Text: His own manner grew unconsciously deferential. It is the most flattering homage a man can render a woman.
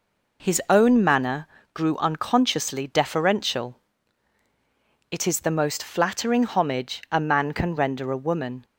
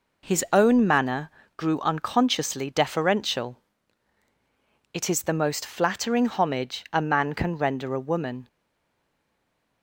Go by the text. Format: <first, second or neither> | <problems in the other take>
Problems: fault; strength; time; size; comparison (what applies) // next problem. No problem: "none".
first | pauses between "manner" and "grew"; slight; at 1.2 s; 0.30 s long; slight in the first // stays silent after the last word; noticeable; from 8.4 s on; 1.4 s long